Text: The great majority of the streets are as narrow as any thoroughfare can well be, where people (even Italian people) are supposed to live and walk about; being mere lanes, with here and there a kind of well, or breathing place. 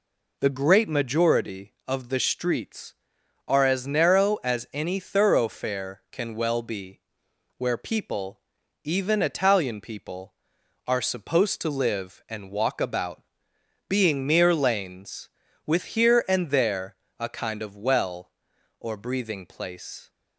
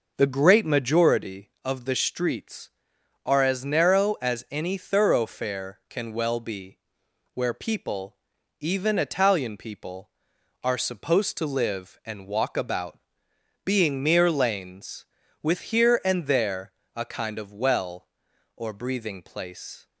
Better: first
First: pauses between "there" and "a"; slight; at 16.9 s; 0.24 s long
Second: starts louder than the rest; noticeable; until 1.3 s; 5.5 dB // pauses between "there" and "a"; slight; at 16.7 s; 0.24 s long

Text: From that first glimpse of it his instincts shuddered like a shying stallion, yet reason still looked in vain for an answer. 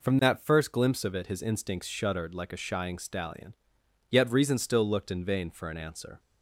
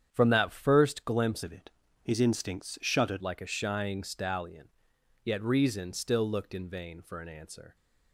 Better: first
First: none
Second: starts louder than the rest; strong; until 1.1 s; 8.5 dB // changes voice from "of" to "shuddered"; from 1.4 to 3.2 s; 1.8 s long // pauses between "it" and "his"; slight; at 1.7 s; 0.32 s long

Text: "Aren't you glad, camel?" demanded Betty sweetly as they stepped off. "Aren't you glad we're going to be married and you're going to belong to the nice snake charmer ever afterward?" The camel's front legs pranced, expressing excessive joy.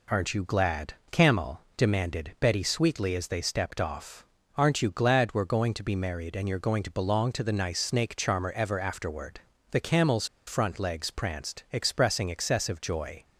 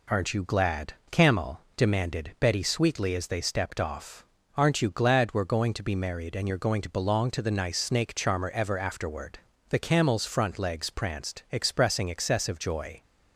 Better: second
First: pauses between "camel's" and "front"; slight; at 10.2 s; 0.22 s long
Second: none

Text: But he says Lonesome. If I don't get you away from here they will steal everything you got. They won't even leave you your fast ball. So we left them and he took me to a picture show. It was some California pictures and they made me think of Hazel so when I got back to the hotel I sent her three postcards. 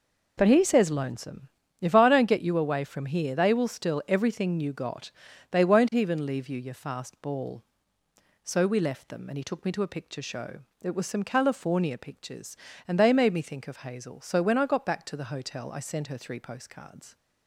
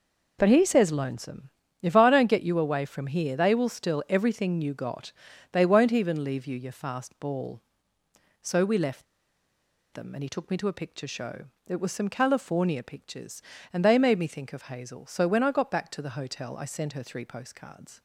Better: first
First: none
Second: pauses between "left" and "them"; noticeable; at 9.0 s; 0.90 s long

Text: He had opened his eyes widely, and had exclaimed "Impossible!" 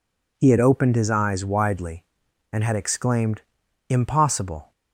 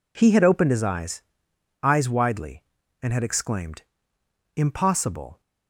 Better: first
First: pauses between "exclaimed" and "Impossible"; noticeable; at 3.4 s; 0.48 s long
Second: says "eyes" twice; at 1.8 s // pauses between "exclaimed" and "Impossible"; noticeable; at 3.8 s; 0.74 s long

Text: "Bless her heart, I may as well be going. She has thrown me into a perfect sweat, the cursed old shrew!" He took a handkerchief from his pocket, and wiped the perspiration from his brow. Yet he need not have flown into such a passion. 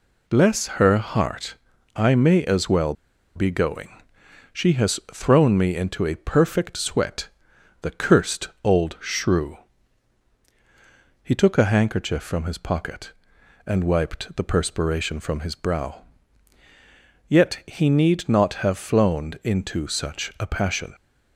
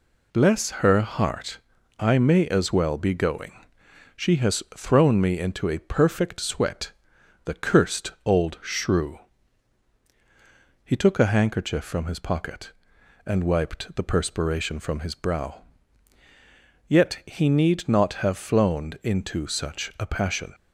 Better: second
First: pauses between "well" and "be"; at 2.9 s; 0.42 s long // pauses between "cursed" and "old"; slight; at 8.4 s; 0.16 s long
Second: none

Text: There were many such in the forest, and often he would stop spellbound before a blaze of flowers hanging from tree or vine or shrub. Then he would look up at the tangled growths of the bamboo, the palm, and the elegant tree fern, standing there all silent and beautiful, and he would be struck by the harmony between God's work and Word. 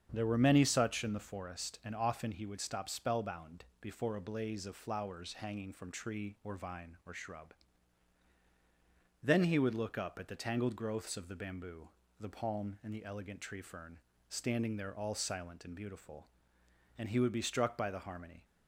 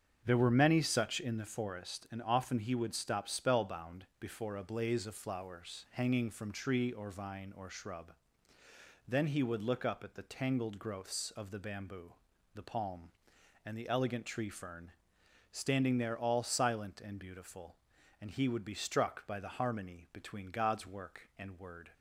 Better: second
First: starts louder than the rest; strong; until 1.1 s; 7.5 dB // pauses between "spellbound" and "before"; slight; at 3.6 s; 0.16 s long // stops before "between God's work and Word"; at 18.4 s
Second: starts louder than the rest; strong; until 1.2 s; 7.5 dB

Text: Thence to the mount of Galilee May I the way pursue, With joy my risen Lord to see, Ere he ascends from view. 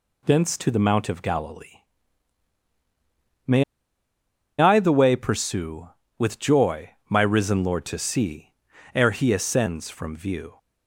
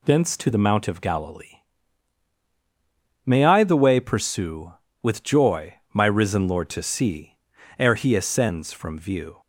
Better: second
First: pauses between "Galilee" and "May"; strong; at 1.8 s; 1.6 s long // pauses between "May" and "I"; noticeable; at 3.6 s; 0.95 s long // pauses between "joy" and "my"; slight; at 6.8 s; 0.20 s long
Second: pauses between "Galilee" and "May"; strong; at 1.5 s; 1.6 s long // pauses between "joy" and "my"; slight; at 5.7 s; 0.20 s long

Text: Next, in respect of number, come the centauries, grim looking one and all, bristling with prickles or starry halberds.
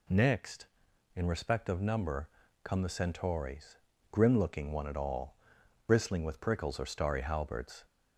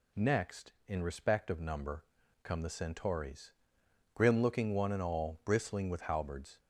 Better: first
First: none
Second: skips "prickles or starry"; at 6.0 s

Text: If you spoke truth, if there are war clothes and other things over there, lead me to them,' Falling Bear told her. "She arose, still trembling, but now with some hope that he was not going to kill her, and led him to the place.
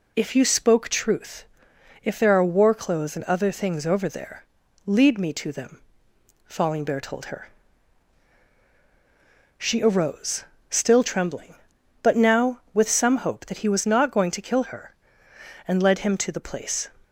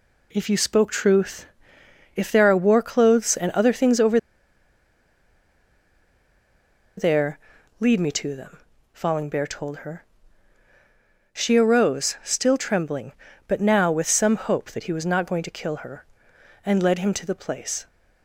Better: first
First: none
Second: pauses between "over" and "there"; strong; at 4.1 s; 2.7 s long

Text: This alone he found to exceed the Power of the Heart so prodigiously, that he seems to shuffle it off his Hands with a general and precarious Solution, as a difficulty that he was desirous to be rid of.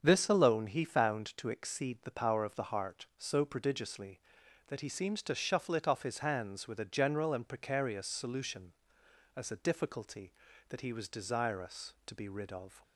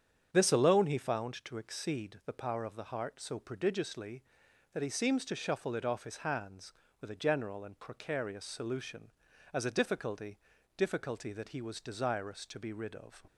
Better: first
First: starts louder than the rest; strong; until 1.0 s; 7 dB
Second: starts louder than the rest; strong; until 1.3 s; 8 dB // says "difficulty" twice; at 10.7 s

